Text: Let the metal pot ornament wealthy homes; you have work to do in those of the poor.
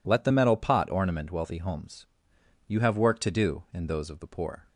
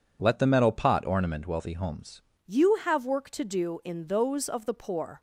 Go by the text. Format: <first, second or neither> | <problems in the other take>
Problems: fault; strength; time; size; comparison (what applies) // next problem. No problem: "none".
first | changes voice at "you"; from 2.4 s on; 2.7 s long